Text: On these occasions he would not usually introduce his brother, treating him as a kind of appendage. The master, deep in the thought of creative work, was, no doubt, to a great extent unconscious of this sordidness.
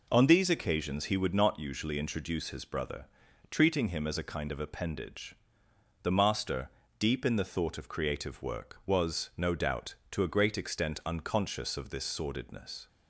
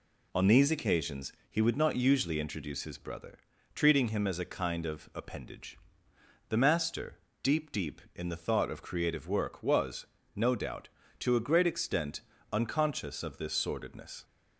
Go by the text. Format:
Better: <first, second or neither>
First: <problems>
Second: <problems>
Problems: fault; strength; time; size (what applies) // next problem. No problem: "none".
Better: first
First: none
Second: pauses between "occasions" and "he"; slight; at 1.3 s; 0.18 s long // says "deep" twice; at 7.7 s // pauses between "extent" and "unconscious"; slight; at 12.2 s; 0.32 s long